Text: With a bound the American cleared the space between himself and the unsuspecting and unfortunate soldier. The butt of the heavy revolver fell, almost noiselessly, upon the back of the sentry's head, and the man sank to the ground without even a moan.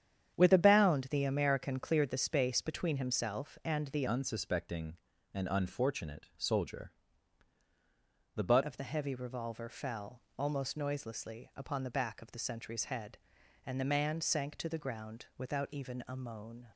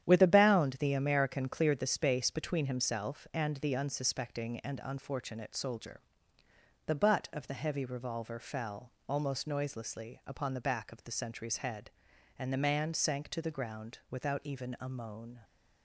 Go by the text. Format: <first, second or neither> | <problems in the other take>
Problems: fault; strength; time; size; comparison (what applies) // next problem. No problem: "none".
second | starts louder than the rest; strong; until 1.4 s; 9 dB; strong in the second // changes voice from "unsuspecting" to "butt"; from 4.0 to 8.6 s; 4.6 s long